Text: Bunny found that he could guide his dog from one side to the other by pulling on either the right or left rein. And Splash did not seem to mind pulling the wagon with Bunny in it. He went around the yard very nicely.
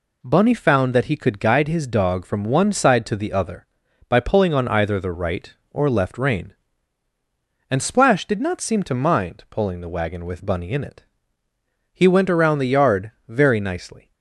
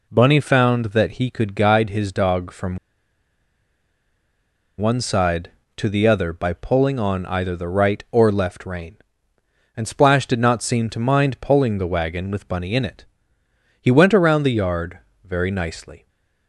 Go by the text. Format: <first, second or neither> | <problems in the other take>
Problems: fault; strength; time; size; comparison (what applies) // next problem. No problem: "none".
first | pauses between "from" and "one"; strong; at 2.7 s; 2.0 s long // pauses between "yard" and "very"; slight; at 14.9 s; 0.24 s long; slight in the first // stays silent after the last word; slight; from 15.9 s on; 0.5 s long